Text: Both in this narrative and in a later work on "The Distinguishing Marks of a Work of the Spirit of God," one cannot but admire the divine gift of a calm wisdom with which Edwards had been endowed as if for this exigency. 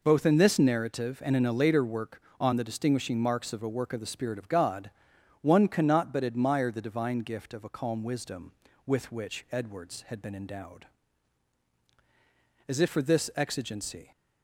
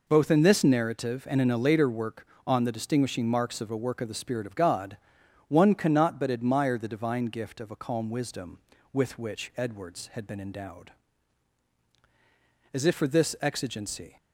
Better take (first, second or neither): neither